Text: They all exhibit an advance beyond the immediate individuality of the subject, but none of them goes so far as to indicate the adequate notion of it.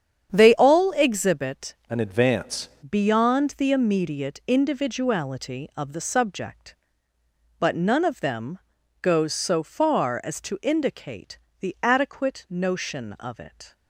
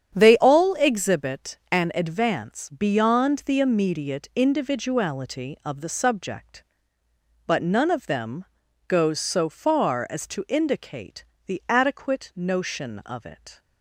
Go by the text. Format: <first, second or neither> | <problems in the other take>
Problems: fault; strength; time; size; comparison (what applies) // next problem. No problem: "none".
second | starts louder than the rest; strong; until 1.3 s; 8 dB; strong in the second // changes voice from "an" to "advance"; from 1.8 to 2.6 s; 0.8 s long // pauses between "them" and "goes"; noticeable; at 8.5 s; 0.46 s long; noticeable in the second // pauses between "indicate" and "the"; slight; at 11.3 s; 0.22 s long; slight in the second